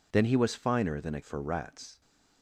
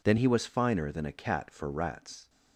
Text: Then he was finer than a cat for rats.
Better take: second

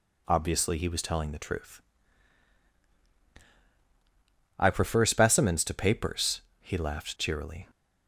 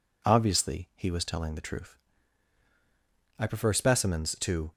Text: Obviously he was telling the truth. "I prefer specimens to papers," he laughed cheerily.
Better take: first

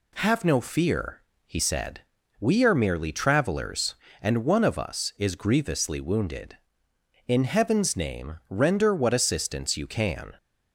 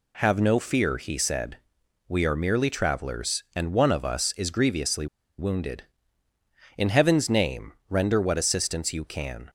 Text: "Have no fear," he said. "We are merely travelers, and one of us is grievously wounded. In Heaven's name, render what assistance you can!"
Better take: first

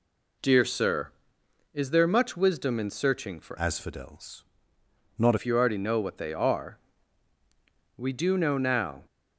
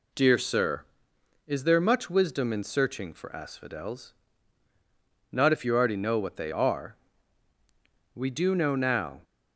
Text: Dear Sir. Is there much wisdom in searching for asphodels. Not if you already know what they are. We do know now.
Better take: second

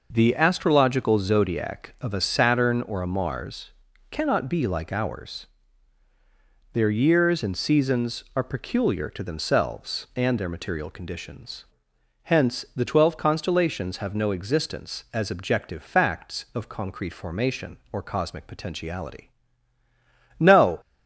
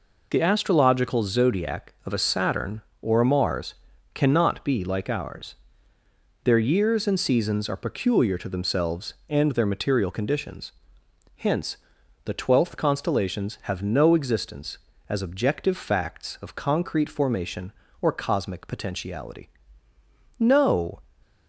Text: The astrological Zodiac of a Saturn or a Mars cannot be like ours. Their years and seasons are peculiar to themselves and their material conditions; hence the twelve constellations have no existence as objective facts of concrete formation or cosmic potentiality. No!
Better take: first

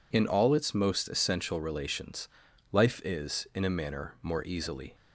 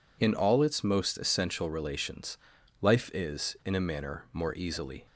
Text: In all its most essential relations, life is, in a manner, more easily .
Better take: neither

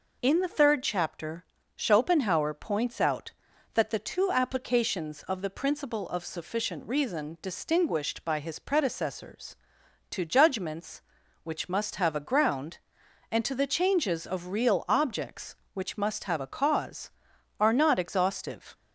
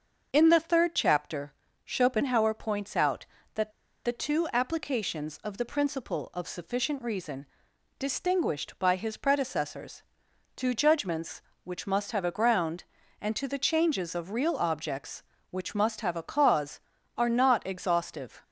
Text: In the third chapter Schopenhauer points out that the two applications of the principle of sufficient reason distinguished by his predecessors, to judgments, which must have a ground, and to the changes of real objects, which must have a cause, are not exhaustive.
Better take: first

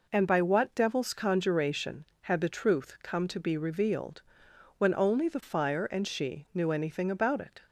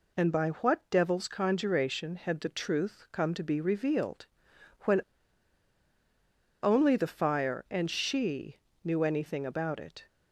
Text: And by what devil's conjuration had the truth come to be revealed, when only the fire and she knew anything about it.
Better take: first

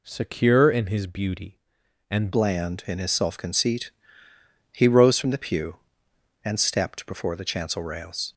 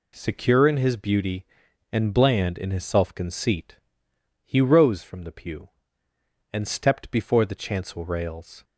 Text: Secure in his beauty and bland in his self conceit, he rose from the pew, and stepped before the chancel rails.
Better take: second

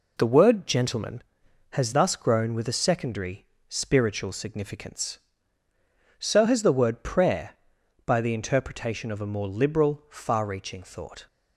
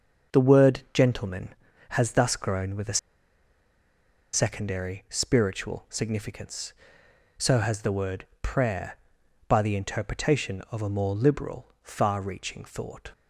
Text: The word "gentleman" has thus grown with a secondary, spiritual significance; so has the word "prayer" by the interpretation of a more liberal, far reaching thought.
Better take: first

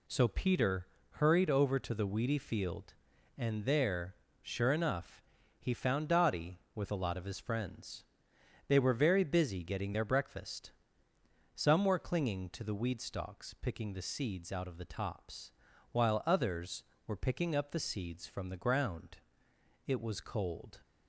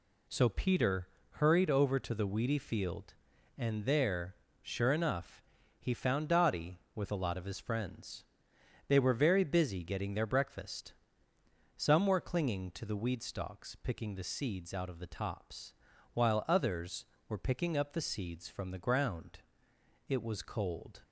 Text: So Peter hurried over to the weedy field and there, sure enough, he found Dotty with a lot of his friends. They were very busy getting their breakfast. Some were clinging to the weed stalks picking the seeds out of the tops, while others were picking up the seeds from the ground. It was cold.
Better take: neither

